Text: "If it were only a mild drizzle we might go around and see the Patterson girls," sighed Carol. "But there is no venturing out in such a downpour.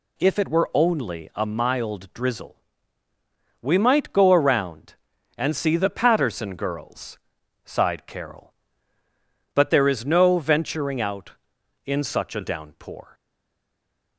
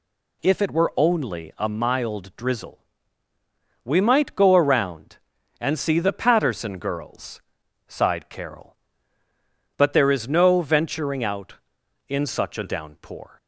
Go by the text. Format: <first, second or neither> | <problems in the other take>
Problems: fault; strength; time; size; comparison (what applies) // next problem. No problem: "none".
second | pauses between "drizzle" and "we"; at 2.5 s; 1.0 s long; also in the second // stays silent after the last word; from 13.1 s on; 1.0 s long